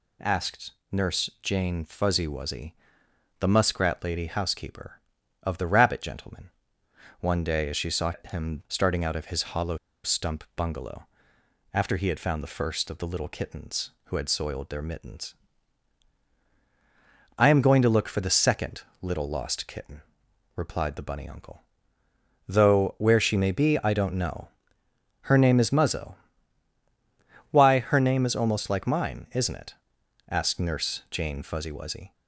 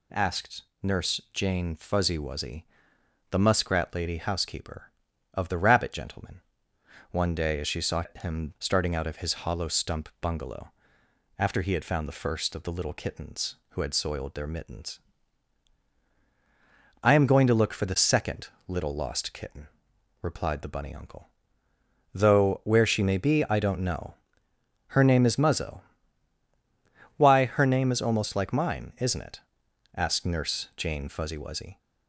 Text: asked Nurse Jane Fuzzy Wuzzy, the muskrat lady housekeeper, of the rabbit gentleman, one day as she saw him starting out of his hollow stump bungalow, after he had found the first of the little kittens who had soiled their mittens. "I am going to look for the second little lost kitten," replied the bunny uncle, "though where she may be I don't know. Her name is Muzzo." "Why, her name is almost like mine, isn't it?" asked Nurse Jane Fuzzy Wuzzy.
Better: second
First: pauses between "asked" and "Nurse"; slight; at 0.7 s; 0.20 s long // pauses between "saw" and "him"; slight; at 8.1 s; 0.18 s long // pauses between "hollow" and "stump"; slight; at 9.7 s; 0.27 s long // pauses between "second" and "little"; slight; at 18.8 s; 0.20 s long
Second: pauses between "asked" and "Nurse"; slight; at 0.6 s; 0.20 s long // pauses between "saw" and "him"; slight; at 8.0 s; 0.18 s long // pauses between "second" and "little"; slight; at 18.4 s; 0.20 s long

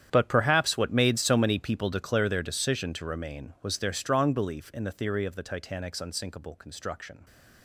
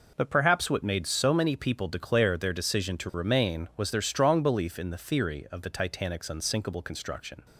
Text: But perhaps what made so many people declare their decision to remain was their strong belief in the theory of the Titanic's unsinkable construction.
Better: second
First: gets quieter; strong; throughout; 17 dB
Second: none

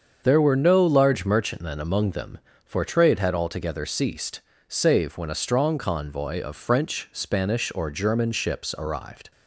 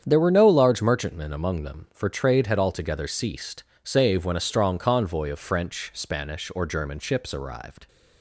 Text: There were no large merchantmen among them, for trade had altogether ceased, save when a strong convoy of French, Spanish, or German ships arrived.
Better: neither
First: starts louder than the rest; until 1.2 s; 7 dB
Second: starts louder than the rest; strong; until 1.0 s; 8 dB

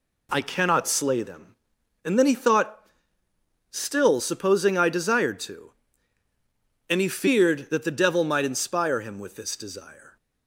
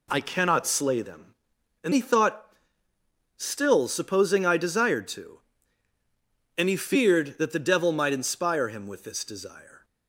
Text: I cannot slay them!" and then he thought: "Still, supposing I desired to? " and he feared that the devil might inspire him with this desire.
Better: first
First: none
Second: skips "then"; at 1.9 s

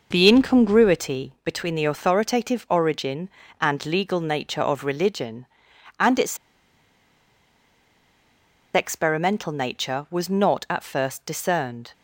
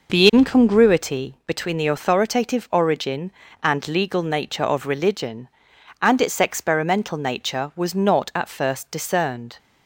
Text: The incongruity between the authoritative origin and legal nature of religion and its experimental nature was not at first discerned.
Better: second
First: pauses between "its" and "experimental"; strong; at 6.3 s; 2.3 s long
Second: none

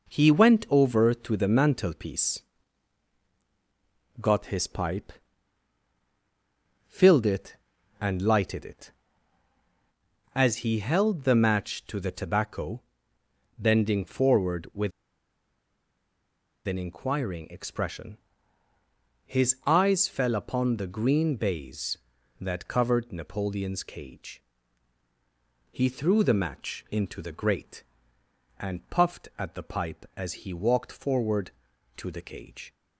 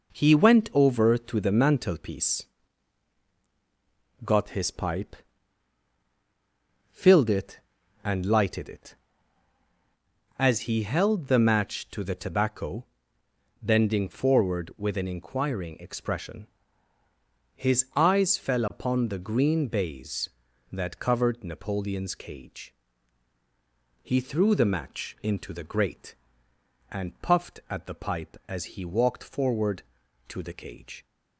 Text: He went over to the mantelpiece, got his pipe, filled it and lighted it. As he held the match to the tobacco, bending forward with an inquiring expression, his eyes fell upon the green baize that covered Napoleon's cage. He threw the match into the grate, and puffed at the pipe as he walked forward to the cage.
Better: second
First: pauses between "with" and "an"; strong; at 14.9 s; 1.7 s long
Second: none

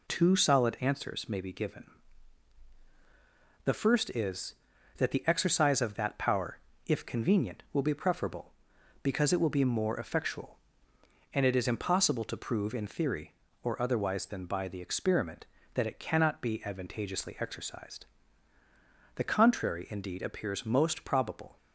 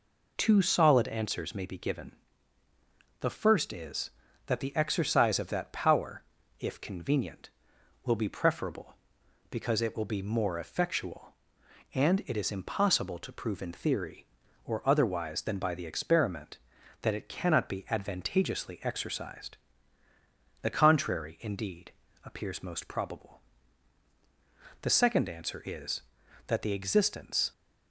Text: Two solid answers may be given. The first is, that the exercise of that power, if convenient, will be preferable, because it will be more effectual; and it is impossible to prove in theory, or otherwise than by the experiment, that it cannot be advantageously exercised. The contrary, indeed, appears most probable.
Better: first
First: none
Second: goes on to say "The second answer is that the existence"; strong; from 24.8 s on; 2.7 s long

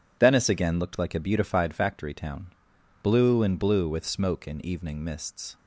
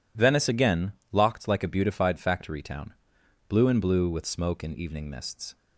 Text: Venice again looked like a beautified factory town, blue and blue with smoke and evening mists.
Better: first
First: none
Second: says "locked" for "looked"; at 1.1 s

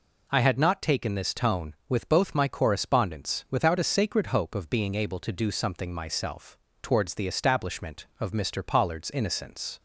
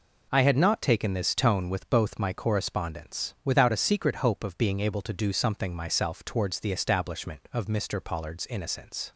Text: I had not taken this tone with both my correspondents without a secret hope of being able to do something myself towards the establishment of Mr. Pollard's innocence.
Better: second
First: says "sacred" for "secret"; at 3.8 s // pauses between "myself" and "towards"; slight; at 6.5 s; 0.24 s long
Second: none

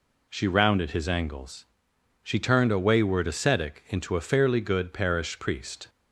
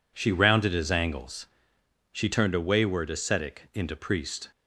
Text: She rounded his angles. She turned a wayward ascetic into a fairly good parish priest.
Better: first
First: none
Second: skips "a fairly good parish"; at 3.9 s

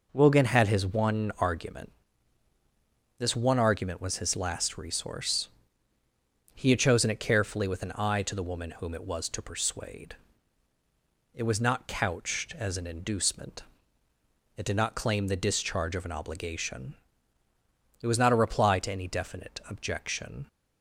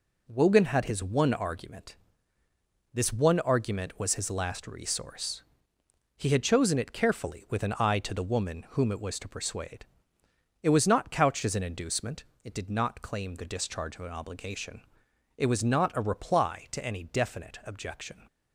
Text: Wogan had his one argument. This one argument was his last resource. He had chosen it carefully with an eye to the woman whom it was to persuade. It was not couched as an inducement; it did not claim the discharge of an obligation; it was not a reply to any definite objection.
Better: neither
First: none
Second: none

